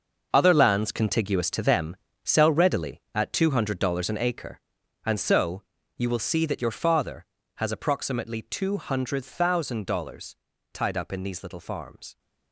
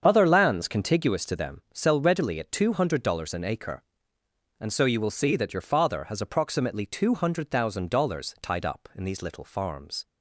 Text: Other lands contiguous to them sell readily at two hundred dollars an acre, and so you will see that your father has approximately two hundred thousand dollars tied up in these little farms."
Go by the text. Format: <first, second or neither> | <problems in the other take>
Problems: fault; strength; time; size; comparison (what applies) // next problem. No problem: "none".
second | gets quieter; strong; throughout; 12 dB // starts louder than the rest; noticeable; until 1.3 s; 6 dB; strong in the second // pauses between "them" and "sell"; slight; at 1.9 s; 0.26 s long // pauses between "so" and "you"; slight; at 5.6 s; 0.34 s long // pauses between "dollars" and "tied"; at 10.3 s; 0.38 s long